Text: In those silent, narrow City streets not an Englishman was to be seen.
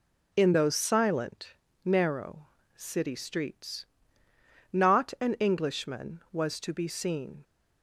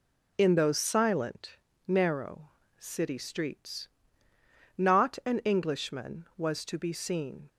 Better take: neither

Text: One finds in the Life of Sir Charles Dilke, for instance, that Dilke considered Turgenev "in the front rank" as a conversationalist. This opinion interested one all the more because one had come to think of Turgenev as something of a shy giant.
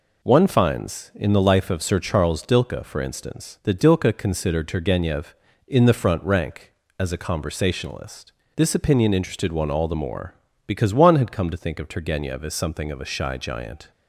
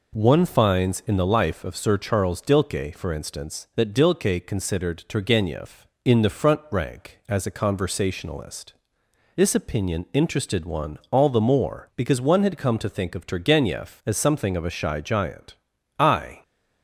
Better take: first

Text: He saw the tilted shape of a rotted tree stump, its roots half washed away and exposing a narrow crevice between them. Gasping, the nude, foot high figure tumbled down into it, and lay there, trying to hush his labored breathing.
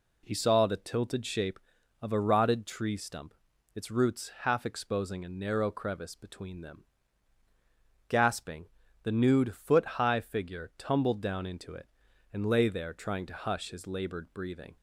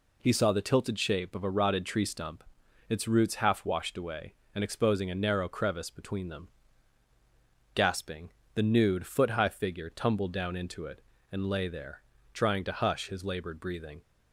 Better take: second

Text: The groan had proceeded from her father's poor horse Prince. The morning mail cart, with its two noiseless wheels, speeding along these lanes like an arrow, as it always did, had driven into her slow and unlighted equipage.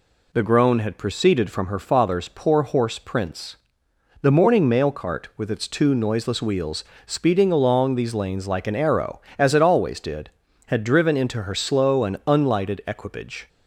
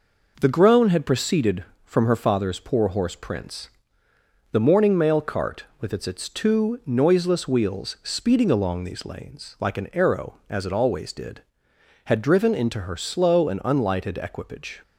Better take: first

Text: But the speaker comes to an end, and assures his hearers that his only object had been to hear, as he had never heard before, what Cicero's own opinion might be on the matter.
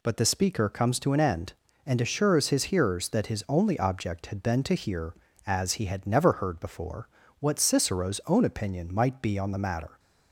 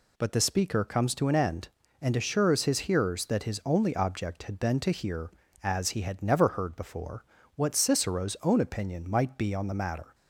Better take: neither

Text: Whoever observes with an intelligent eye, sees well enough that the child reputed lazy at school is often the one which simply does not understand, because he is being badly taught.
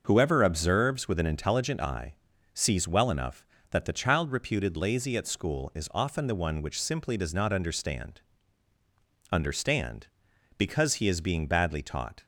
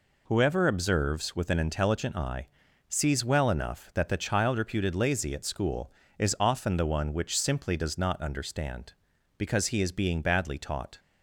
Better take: second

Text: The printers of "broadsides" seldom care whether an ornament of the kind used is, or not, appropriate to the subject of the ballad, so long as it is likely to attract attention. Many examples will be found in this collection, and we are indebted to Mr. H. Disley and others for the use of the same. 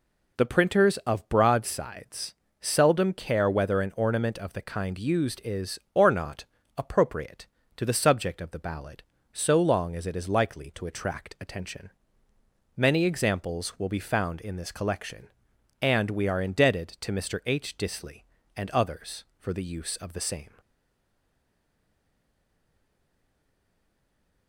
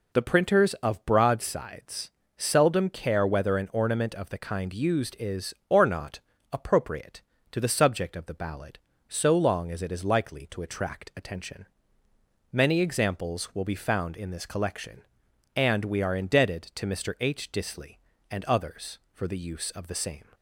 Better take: second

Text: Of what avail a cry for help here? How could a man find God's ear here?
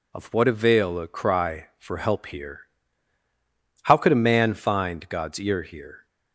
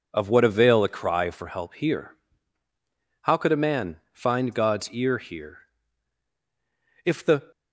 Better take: first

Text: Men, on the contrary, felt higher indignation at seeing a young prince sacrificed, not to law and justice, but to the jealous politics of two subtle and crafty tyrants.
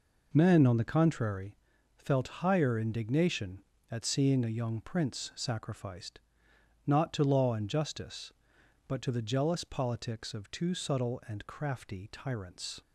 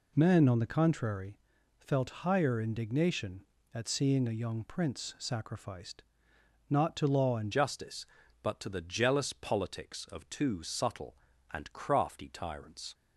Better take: first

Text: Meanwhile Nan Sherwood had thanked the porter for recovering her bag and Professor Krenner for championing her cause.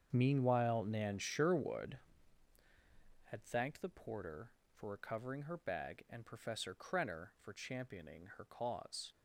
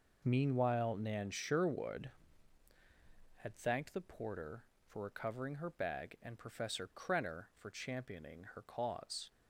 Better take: second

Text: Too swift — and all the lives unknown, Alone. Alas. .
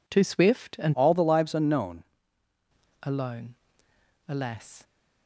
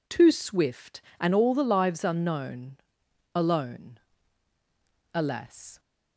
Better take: second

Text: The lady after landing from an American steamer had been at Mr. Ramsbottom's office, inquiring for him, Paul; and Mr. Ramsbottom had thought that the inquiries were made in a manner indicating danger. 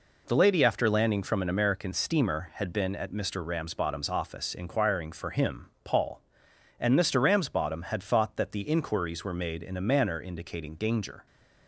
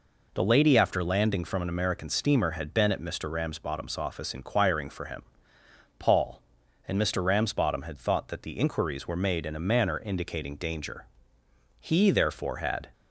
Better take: first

